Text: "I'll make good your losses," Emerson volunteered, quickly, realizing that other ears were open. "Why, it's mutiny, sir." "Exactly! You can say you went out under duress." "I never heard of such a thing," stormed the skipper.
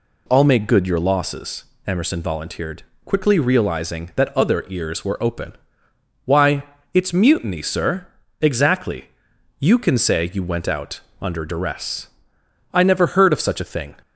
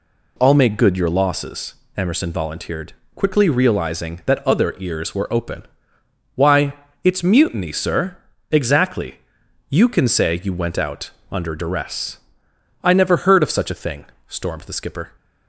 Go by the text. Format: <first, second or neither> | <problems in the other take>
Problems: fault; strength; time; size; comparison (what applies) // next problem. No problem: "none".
second | pauses between "out" and "under"; slight; at 10.9 s; 0.22 s long; slight in the second // stops before "stormed the skipper"; at 14.0 s